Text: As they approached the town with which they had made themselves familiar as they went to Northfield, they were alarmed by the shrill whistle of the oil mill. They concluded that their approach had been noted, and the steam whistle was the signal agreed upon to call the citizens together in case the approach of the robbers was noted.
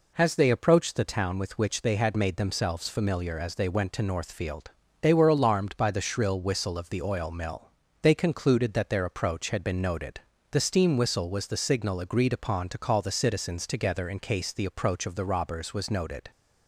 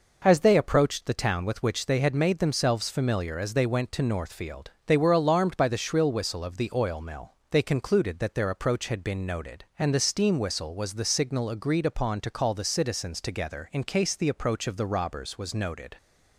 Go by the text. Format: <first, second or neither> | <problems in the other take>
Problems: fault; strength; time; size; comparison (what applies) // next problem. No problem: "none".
second | skips "and"; at 10.3 s